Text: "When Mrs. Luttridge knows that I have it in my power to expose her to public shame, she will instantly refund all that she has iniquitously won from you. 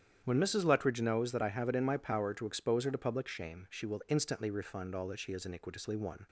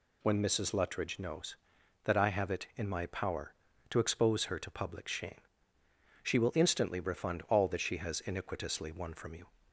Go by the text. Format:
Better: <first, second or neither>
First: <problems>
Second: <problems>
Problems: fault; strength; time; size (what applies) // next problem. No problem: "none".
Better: second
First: starts louder than the rest; strong; until 1.2 s; 9 dB // stops before "from you"; at 6.2 s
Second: none